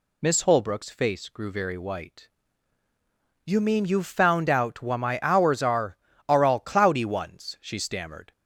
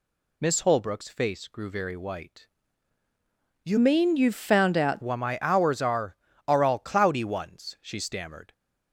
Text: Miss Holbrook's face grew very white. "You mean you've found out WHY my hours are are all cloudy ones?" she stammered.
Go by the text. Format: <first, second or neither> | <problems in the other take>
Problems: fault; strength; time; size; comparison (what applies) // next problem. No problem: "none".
first | changes voice from "mean" to "out"; from 3.7 to 5.0 s; 1.3 s long